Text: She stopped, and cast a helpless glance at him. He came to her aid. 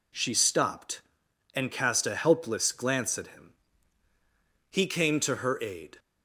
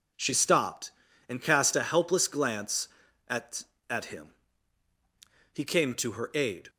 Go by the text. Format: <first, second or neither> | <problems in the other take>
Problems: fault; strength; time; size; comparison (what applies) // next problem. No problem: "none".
first | says "at" twice; at 3.8 s